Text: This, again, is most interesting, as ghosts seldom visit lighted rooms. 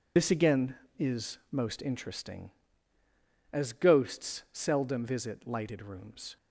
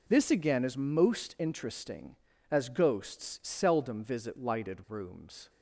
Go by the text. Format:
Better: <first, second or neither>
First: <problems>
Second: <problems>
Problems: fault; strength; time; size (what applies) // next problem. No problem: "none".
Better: second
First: loses the start of "This"; at 0.1 s; 70 ms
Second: none